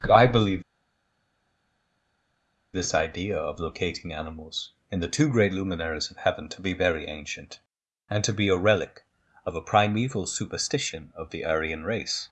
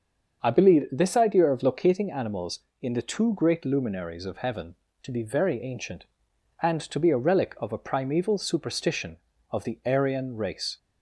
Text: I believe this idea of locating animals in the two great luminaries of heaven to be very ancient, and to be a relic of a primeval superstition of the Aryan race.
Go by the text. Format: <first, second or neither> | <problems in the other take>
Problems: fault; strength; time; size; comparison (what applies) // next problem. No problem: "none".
second | starts louder than the rest; until 3.2 s; 6 dB; also in the second // pauses between "believe" and "this"; strong; at 0.6 s; 2.1 s long